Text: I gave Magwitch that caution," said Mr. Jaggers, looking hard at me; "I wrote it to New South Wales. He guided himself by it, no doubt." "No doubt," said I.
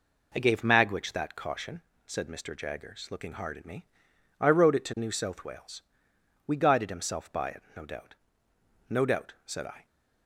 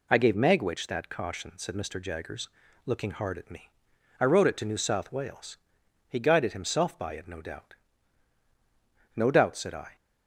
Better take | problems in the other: second | says "We" for "He"; at 6.4 s

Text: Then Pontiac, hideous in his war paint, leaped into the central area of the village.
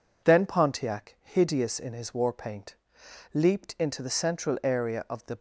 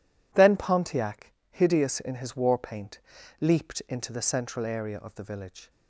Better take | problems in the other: second | stops before "village"; at 5.3 s

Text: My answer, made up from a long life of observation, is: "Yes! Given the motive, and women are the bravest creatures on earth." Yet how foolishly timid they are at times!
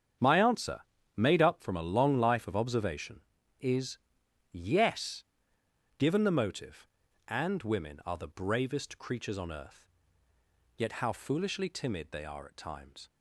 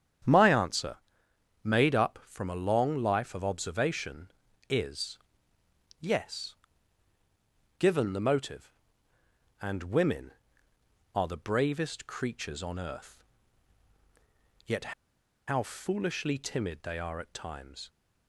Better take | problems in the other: first | starts louder than the rest; strong; until 1.9 s; 9 dB; strong in the first // pauses between "Yet" and "how"; noticeable; at 14.9 s; 0.54 s long

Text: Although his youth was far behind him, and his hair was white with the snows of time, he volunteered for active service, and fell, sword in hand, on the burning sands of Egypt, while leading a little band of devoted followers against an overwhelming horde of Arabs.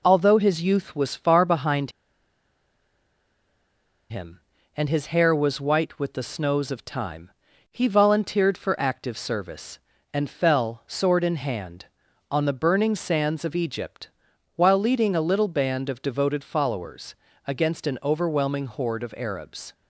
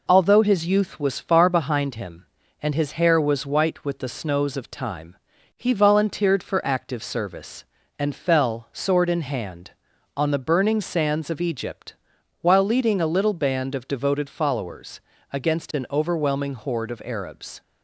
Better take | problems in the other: second | pauses between "behind" and "him"; strong; at 1.9 s; 2.1 s long // pauses between "followers" and "against"; slight; at 17.1 s; 0.32 s long; slight in the second

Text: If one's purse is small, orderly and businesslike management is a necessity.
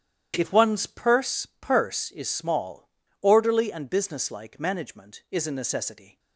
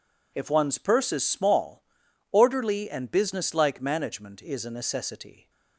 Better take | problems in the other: second | starts louder than the rest; strong; until 1.3 s; 10 dB // says "purse" twice; at 1.6 s

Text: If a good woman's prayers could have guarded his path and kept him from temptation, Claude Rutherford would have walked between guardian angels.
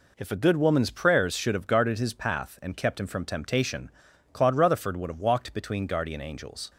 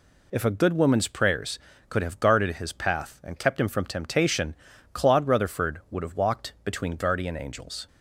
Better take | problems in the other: second | says "should" for "could"; at 1.3 s

